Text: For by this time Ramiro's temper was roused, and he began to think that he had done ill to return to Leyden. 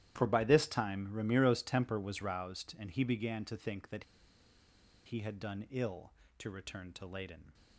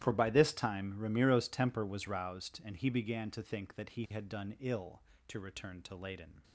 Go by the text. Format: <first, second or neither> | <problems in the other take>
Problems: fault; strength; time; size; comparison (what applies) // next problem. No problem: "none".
second | starts louder than the rest; strong; until 1.1 s; 12 dB; strong in the second // pauses between "that" and "he"; at 4.0 s; 1.0 s long